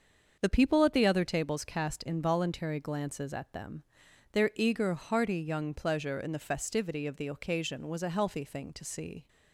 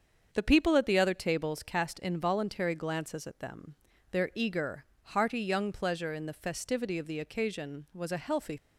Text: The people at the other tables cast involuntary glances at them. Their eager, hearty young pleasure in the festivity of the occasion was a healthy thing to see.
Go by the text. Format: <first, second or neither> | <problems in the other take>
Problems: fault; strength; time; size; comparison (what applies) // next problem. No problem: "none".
first | starts louder than the rest; until 1.3 s; 7 dB; also in the first // stops before "thing to see"; at 8.5 s